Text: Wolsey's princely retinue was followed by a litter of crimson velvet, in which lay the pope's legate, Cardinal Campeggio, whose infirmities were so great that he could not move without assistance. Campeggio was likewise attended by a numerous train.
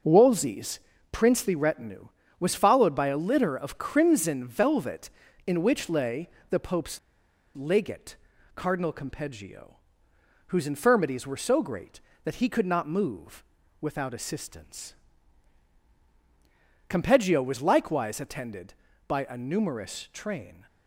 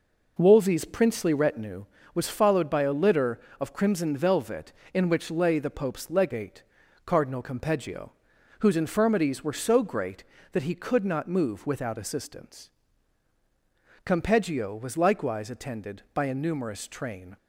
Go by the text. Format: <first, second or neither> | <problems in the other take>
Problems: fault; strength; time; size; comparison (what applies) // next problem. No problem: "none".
second | pauses between "Wolsey's" and "princely"; slight; at 0.7 s; 0.32 s long // pauses between "lay" and "the"; slight; at 6.2 s; 0.22 s long // pauses between "pope's" and "legate"; noticeable; at 6.9 s; 0.56 s long // pauses between "move" and "without"; at 13.4 s; 0.38 s long